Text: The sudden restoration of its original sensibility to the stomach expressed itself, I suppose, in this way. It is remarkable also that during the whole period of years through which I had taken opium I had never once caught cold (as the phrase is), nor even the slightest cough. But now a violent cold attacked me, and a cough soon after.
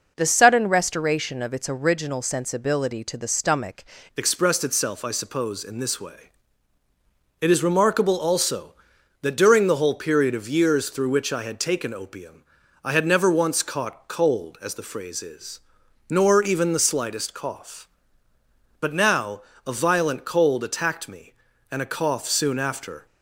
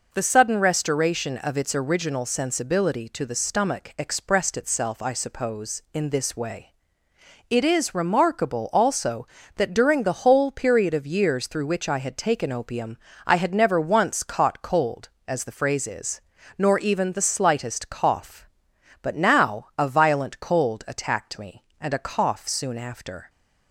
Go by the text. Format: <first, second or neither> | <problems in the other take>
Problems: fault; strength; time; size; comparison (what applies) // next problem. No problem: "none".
second | changes voice at "expressed"; from 4.1 s on; 18.9 s long // pauses between "opium" and "I"; at 12.4 s; 0.40 s long; slight in the second // pauses between "now" and "a"; slight; at 19.4 s; 0.26 s long